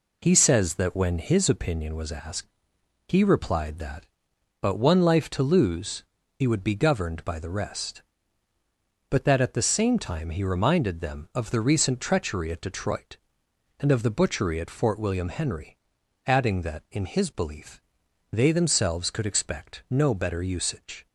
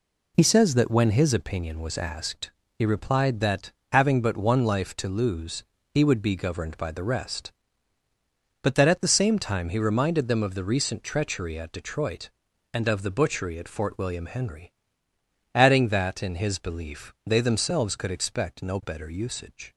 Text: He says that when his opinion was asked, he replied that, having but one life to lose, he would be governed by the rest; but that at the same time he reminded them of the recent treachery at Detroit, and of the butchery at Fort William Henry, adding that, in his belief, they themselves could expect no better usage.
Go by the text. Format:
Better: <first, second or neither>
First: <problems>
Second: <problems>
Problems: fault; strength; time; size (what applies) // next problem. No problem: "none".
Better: second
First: skips "having"; at 4.3 s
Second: none